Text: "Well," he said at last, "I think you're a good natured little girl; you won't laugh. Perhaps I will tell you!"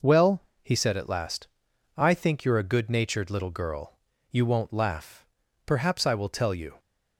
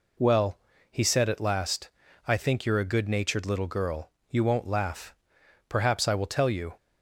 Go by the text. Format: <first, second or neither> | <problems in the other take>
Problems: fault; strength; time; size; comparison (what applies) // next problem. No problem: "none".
neither | none